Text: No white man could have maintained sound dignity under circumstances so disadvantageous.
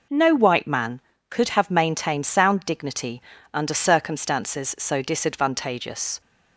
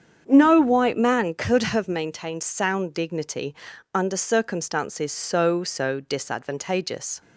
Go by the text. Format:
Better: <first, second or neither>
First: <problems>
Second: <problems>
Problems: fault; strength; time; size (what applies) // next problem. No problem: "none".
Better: first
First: pauses between "dignity" and "under"; slight; at 3.2 s; 0.32 s long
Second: starts louder than the rest; strong; until 1.2 s; 7.5 dB // pauses between "dignity" and "under"; at 3.5 s; 0.38 s long // says "so" twice; at 5.6 s